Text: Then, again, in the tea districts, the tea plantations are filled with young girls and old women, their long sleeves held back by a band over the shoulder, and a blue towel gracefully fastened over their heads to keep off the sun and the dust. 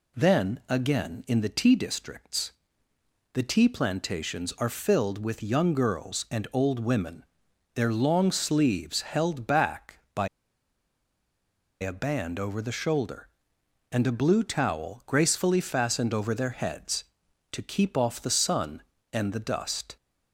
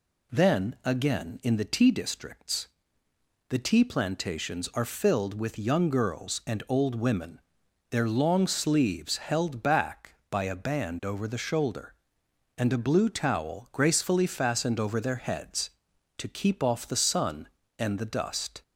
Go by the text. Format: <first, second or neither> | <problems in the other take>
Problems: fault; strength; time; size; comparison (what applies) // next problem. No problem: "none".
second | pauses between "by" and "a"; strong; at 10.2 s; 1.5 s long